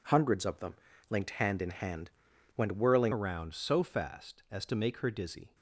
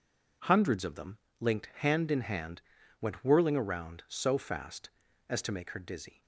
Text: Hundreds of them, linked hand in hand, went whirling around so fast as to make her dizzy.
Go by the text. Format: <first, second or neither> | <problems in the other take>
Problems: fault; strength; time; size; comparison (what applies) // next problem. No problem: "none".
second | changes voice at "around"; from 3.1 s on; 2.4 s long